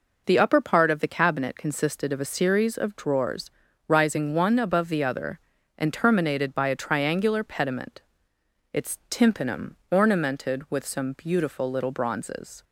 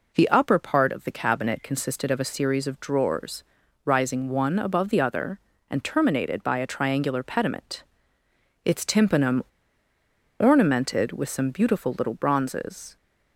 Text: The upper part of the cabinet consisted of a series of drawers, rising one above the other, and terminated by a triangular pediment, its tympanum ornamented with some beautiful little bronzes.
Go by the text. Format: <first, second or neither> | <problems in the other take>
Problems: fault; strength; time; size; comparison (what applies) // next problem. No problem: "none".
first | pauses between "tympanum" and "ornamented"; noticeable; at 9.4 s; 0.97 s long